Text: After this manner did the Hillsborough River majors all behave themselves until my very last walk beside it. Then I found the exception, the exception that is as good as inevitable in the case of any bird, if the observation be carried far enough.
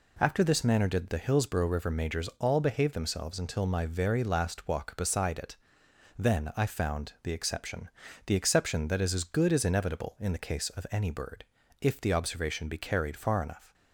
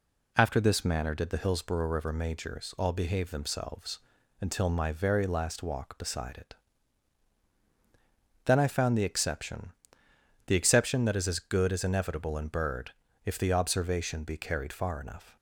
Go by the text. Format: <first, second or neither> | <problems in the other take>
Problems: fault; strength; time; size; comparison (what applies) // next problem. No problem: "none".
first | pauses between "themselves" and "until"; at 3.9 s; 0.42 s long // skips "the case of any"; at 12.4 s